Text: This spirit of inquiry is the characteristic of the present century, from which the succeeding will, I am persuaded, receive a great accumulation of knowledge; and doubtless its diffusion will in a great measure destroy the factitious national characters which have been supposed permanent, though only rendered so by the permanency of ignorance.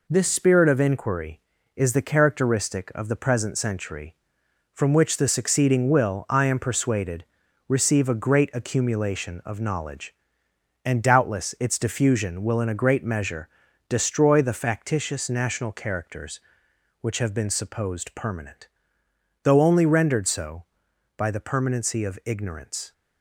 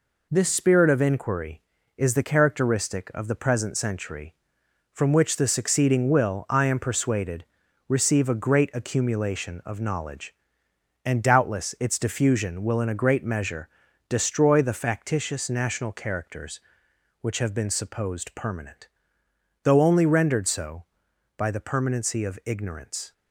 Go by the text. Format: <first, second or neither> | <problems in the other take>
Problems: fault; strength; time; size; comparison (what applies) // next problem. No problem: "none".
neither | pauses between "measure" and "destroy"; the same in both